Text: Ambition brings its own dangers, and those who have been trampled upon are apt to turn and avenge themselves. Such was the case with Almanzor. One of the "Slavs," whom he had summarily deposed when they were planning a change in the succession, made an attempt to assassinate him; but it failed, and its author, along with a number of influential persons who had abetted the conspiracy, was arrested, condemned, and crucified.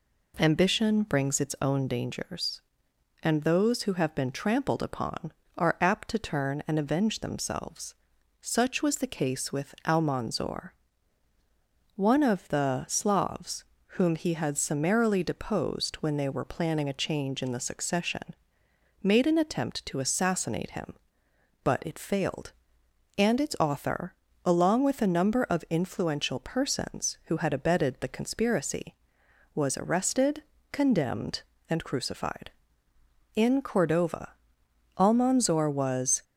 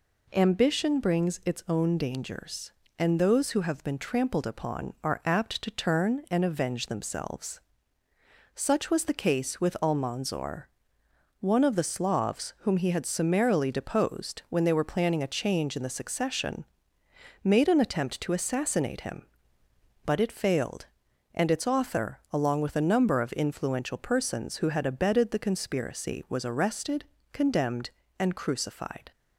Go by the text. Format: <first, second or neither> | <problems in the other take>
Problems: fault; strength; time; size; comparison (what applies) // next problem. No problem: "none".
second | goes on to say "In Cordova Almanzor was"; strong; from 33.3 s on; 2.8 s long